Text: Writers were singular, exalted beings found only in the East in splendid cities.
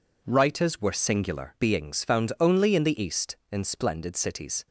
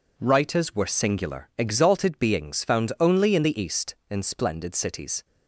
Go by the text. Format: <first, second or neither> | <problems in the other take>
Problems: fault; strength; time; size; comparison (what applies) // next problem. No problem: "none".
second | skips "exalted"; at 1.5 s